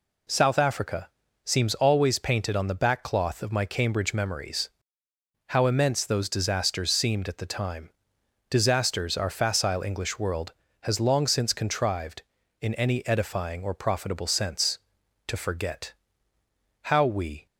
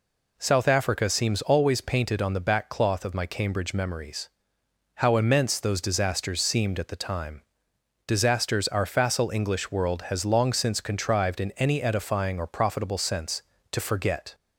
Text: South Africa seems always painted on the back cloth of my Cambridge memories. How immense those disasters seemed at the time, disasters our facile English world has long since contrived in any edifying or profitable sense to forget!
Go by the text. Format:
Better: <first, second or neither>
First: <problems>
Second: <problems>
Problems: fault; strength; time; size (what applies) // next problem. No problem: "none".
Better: second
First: pauses between "Africa" and "seems"; at 1.0 s; 0.38 s long // goes on to say "How we"; noticeable; from 16.8 s on; 0.64 s long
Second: none